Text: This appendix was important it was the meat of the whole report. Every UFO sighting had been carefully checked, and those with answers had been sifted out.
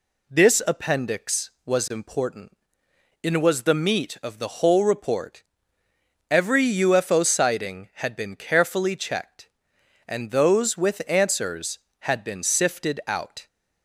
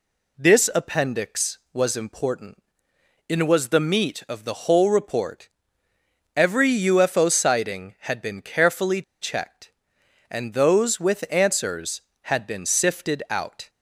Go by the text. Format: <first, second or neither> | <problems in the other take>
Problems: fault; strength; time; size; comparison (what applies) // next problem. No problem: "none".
first | pauses between "important" and "it"; noticeable; at 2.5 s; 0.72 s long; noticeable in the first // pauses between "carefully" and "checked"; slight; at 9.0 s; 0.18 s long